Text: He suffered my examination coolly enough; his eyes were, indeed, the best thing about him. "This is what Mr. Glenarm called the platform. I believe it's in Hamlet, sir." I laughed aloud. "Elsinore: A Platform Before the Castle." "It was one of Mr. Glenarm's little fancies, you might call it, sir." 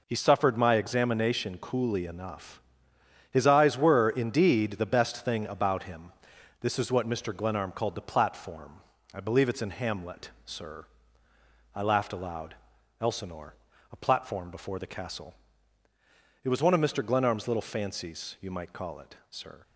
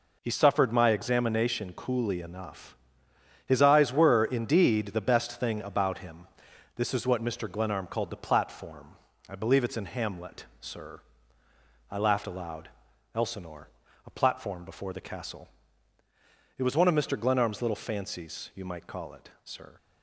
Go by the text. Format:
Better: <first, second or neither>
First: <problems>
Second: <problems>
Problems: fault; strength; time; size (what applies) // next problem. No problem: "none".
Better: neither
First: none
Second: none